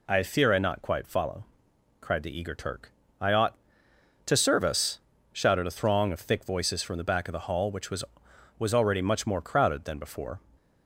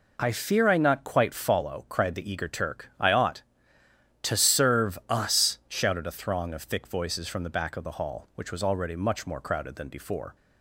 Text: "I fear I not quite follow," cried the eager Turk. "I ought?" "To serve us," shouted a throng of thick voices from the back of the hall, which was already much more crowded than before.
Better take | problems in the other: second | says "was" twice; at 8.5 s

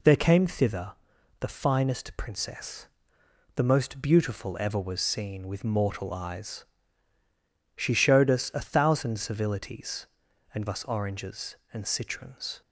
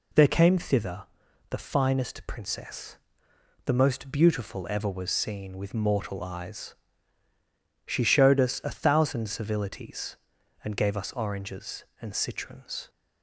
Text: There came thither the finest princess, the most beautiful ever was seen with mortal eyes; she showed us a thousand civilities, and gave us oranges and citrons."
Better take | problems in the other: second | pauses between "thither" and "the"; noticeable; at 0.9 s; 0.48 s long; noticeable in the second // skips "gave"; at 10.6 s

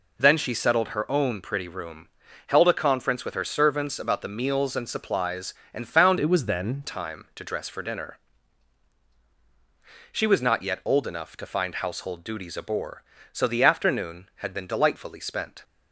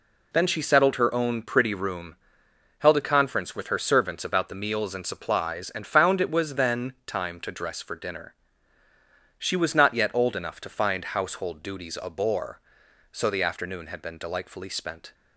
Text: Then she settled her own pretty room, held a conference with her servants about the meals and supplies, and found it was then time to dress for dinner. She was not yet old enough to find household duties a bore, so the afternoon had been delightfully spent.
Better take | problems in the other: second | changes voice from "it" to "then"; from 6.2 to 6.8 s; 0.6 s long

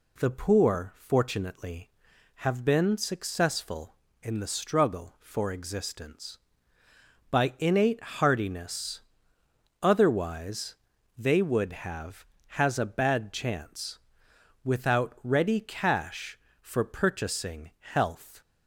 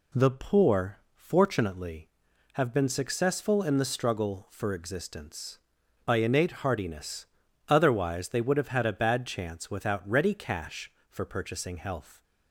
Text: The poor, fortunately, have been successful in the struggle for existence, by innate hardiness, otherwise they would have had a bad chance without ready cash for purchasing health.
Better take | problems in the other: second | pauses between "otherwise" and "they"; at 10.7 s; 0.44 s long // says "has" for "had"; at 12.4 s // pauses between "chance" and "without"; noticeable; at 13.9 s; 0.66 s long

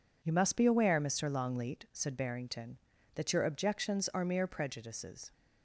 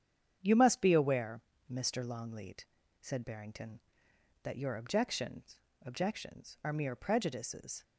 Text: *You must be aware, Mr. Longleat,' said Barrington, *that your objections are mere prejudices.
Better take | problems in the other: first | starts louder than the rest; strong; until 1.4 s; 8.5 dB // says "objections" twice; at 5.8 s

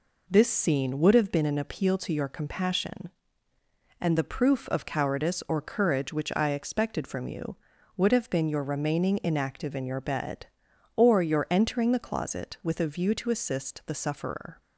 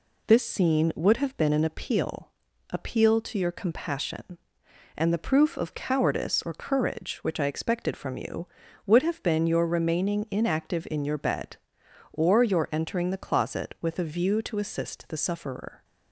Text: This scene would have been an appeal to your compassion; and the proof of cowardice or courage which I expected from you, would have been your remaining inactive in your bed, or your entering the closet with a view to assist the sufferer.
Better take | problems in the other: first | says "appeal" twice; at 2.6 s

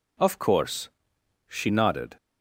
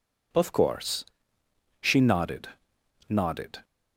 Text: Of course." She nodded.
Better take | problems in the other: first | says "nodded" twice; at 3.0 s

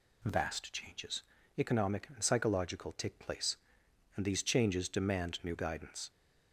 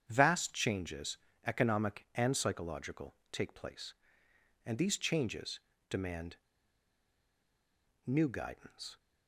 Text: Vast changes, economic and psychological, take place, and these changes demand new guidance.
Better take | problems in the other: first | starts louder than the rest; strong; until 1.0 s; 8.5 dB // pauses between "changes" and "demand"; slight; at 5.5 s; 0.30 s long // pauses between "demand" and "new"; strong; at 6.3 s; 1.6 s long

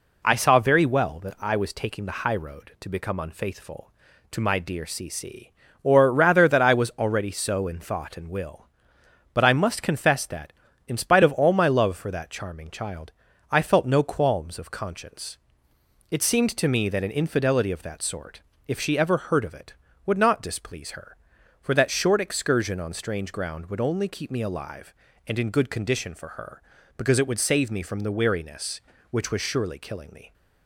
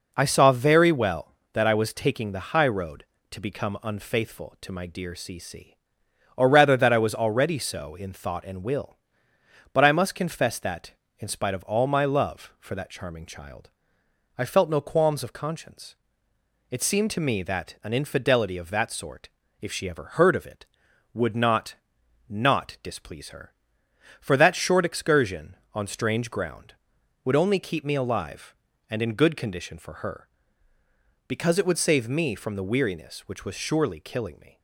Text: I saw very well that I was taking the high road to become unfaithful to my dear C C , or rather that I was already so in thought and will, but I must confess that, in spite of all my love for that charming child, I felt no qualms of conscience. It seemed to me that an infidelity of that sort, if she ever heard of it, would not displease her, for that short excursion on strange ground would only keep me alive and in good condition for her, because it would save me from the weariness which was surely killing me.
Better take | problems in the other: first | says "not" twice; at 22.2 s

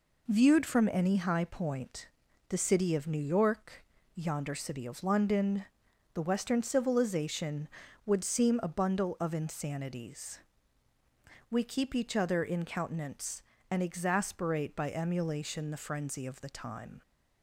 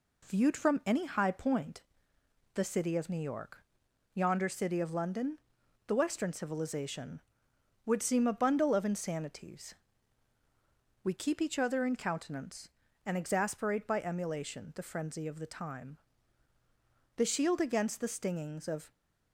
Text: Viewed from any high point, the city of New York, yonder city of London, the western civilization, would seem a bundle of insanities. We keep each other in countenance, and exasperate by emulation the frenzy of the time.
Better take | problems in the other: first | goes on to say "The shield against the stingings of"; strong; from 17.1 s on; 1.7 s long

